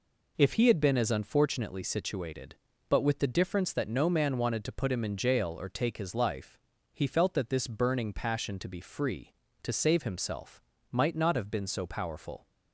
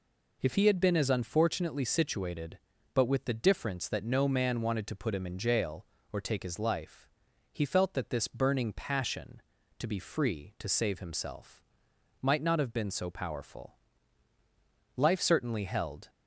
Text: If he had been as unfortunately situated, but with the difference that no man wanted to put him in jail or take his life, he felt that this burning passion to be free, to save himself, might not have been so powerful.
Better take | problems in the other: first | goes on to say "Life certainly held"; noticeable; from 14.9 s on; 1.1 s long

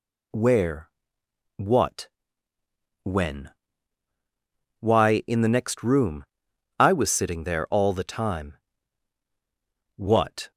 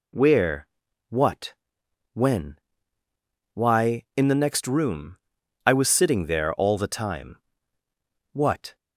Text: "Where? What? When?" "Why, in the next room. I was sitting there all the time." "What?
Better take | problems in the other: neither | none

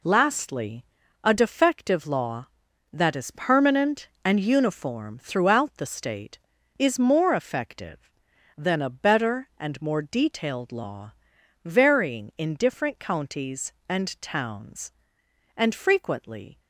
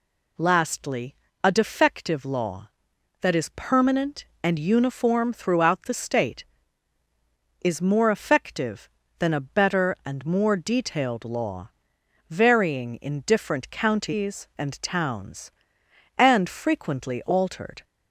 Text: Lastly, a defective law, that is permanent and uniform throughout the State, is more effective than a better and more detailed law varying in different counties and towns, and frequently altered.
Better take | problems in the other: second | pauses between "law" and "varying"; noticeable; at 11.1 s; 0.52 s long; noticeable in the second // stops before "altered"; at 16.5 s

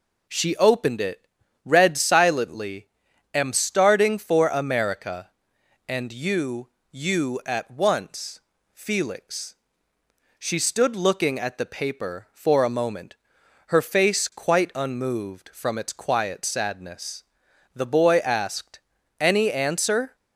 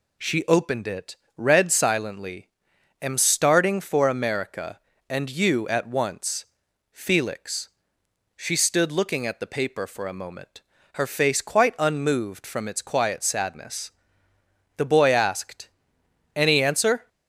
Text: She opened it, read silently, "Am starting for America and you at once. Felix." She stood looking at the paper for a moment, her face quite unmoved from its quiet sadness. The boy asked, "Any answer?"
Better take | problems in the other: second | says "you" twice; at 6.9 s

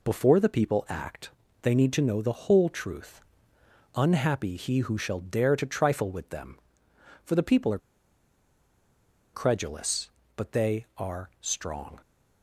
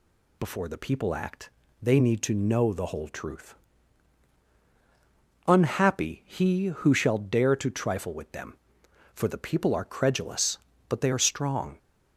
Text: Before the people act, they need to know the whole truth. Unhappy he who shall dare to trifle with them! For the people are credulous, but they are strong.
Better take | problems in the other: second | pauses between "are" and "credulous"; strong; at 7.7 s; 1.5 s long

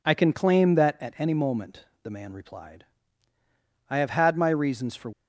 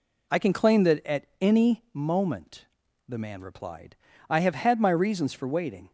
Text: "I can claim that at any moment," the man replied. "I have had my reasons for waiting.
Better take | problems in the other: second | stops before "waiting"; at 5.1 s

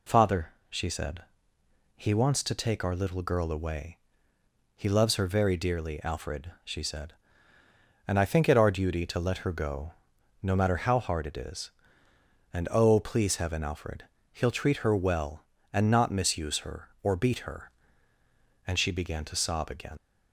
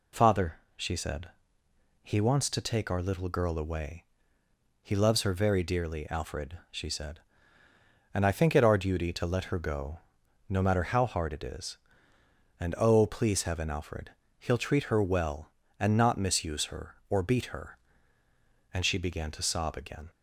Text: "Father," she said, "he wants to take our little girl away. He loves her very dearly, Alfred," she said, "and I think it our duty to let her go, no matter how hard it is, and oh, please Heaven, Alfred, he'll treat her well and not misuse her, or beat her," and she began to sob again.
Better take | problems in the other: second | leaves "again" unfinished; at 19.9 s; 60 ms

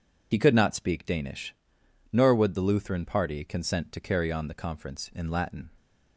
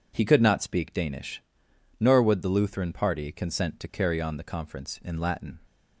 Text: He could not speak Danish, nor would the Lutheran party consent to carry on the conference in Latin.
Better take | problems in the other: second | loses the start of "He"; at 0.3 s; 45 ms

